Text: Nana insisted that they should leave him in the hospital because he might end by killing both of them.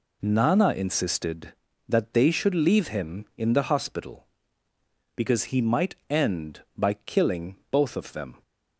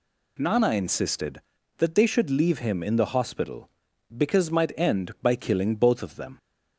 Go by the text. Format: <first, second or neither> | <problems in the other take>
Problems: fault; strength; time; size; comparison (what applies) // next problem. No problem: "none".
first | skips "he"; at 4.5 s